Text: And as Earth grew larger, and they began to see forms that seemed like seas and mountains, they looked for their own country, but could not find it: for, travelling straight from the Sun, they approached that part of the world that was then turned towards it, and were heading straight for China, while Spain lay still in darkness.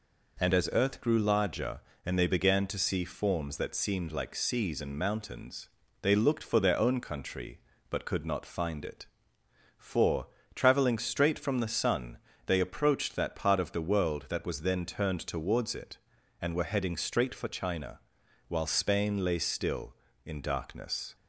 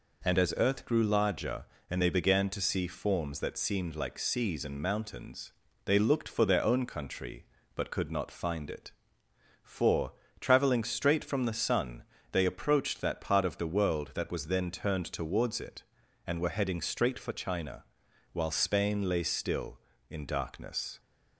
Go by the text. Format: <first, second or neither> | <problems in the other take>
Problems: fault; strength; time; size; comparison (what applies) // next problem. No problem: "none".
neither | none